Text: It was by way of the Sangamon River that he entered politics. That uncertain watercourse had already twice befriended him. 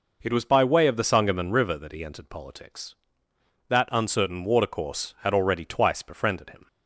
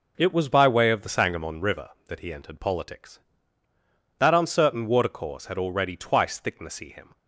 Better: first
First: none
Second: says "thicknessy" for "befriended"; at 6.4 s

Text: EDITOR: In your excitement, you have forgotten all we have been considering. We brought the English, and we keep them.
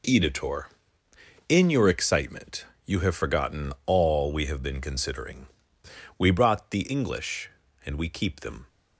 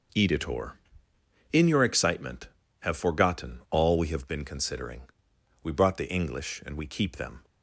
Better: first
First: none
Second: skips "you"; at 2.6 s

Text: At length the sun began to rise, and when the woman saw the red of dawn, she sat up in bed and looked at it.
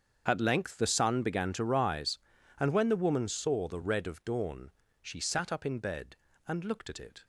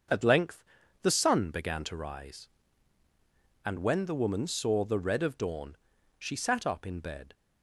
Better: first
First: starts louder than the rest; strong; until 1.2 s; 7 dB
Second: starts louder than the rest; until 1.5 s; 6.5 dB // pauses between "length" and "the"; at 0.6 s; 0.40 s long // stops before "and looked at it"; at 7.3 s

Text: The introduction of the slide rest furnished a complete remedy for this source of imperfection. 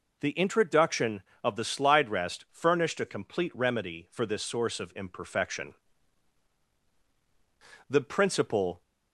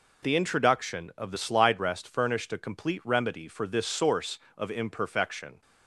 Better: second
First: goes on to say "The principle"; noticeable; from 7.8 s on; 0.92 s long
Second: none

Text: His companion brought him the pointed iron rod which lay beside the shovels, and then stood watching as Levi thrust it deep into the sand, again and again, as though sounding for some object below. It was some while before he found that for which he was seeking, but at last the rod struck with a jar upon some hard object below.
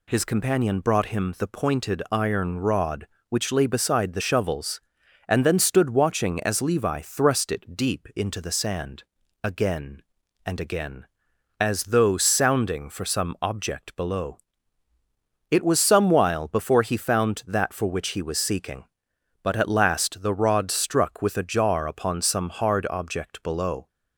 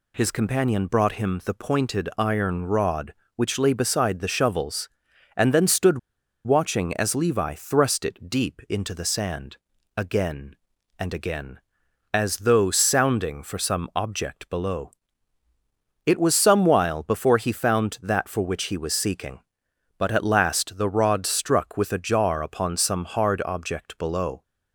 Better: first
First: none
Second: pauses between "stood" and "watching"; noticeable; at 5.9 s; 0.47 s long

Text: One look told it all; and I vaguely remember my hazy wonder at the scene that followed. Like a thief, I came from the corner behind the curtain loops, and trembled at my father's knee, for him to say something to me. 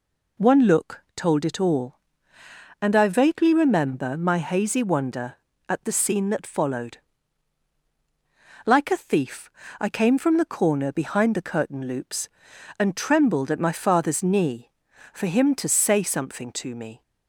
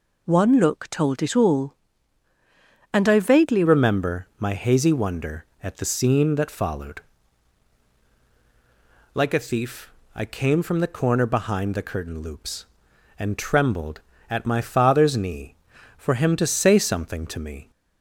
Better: first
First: none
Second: changes voice at "remember"; from 3.6 s on; 14.1 s long

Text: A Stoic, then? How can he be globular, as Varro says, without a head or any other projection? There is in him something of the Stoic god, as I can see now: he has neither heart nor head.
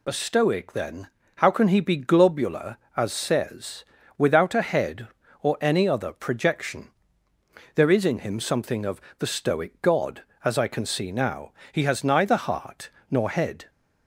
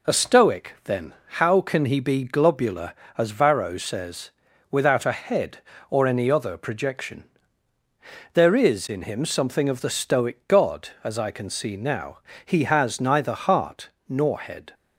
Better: second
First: skips "Varro"; at 3.1 s // pauses between "of" and "the"; slight; at 9.0 s; 0.18 s long // pauses between "heart" and "nor"; slight; at 12.9 s; 0.18 s long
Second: pauses between "heart" and "nor"; slight; at 13.8 s; 0.20 s long

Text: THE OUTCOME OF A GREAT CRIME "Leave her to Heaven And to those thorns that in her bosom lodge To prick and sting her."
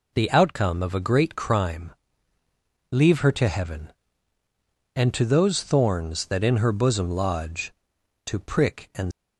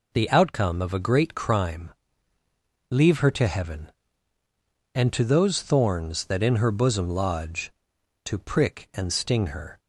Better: second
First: pauses between "CRIME" and "Leave"; at 1.8 s; 1.0 s long // stops before "sting her"; at 9.1 s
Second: pauses between "CRIME" and "Leave"; at 1.8 s; 1.0 s long

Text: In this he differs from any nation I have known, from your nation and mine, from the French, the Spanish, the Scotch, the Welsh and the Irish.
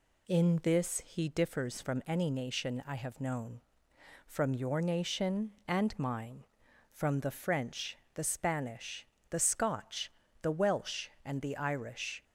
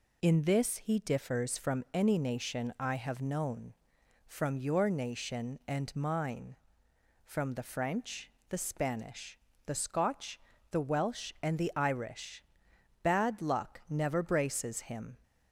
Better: first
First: none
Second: goes on to say "Bad luck never braces him"; strong; from 13.0 s on; 2.1 s long

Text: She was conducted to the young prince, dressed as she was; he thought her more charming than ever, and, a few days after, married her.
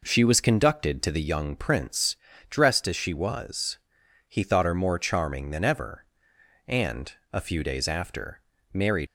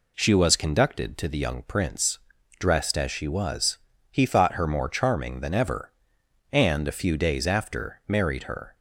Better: second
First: stops before "her"; at 9.0 s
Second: none

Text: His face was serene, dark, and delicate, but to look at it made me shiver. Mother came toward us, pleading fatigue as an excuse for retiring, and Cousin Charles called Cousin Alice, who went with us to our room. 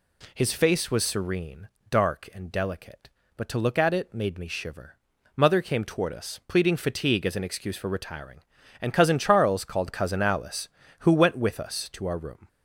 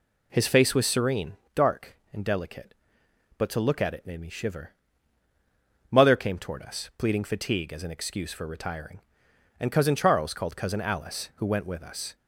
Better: first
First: none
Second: stops before "to our room"; at 12.1 s

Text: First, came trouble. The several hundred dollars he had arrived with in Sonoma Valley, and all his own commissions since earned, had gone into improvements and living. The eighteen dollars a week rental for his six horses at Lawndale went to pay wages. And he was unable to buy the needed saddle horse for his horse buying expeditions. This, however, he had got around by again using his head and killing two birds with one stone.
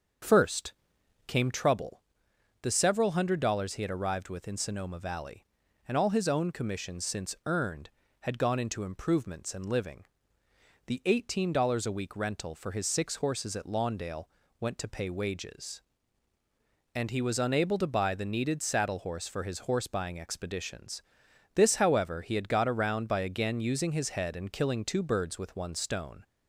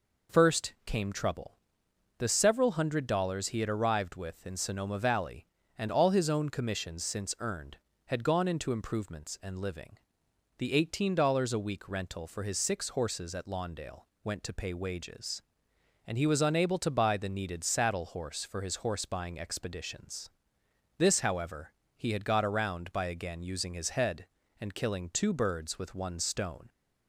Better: second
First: starts louder than the rest; until 1.7 s; 7 dB // pauses between "Lawndale" and "went"; slight; at 14.2 s; 0.34 s long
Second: pauses between "Lawndale" and "went"; slight; at 14.0 s; 0.18 s long

